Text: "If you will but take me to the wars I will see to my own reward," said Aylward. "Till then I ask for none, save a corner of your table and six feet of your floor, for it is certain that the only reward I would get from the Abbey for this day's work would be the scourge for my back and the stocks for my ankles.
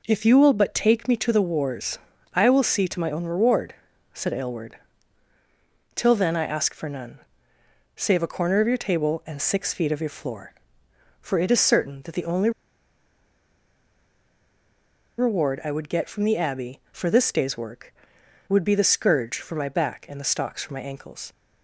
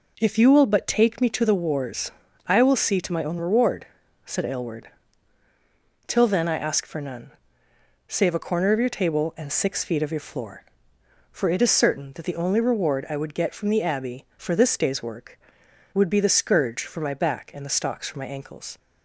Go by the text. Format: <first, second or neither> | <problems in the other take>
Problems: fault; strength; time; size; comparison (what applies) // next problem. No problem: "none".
second | pauses between "wars" and "I"; slight; at 1.9 s; 0.36 s long; slight in the second // pauses between "only" and "reward"; strong; at 12.5 s; 2.6 s long